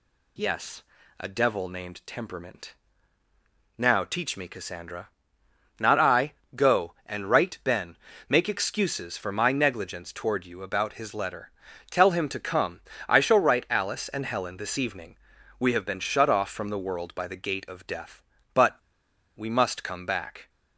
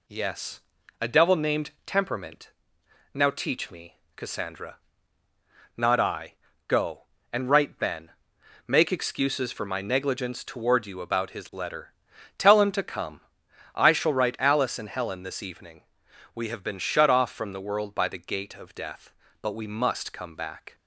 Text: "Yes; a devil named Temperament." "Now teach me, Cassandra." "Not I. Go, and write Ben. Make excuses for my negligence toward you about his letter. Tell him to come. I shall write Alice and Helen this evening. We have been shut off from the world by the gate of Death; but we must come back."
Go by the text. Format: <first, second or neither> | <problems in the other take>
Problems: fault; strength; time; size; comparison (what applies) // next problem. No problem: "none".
second | pauses between "but" and "we"; noticeable; at 18.7 s; 0.61 s long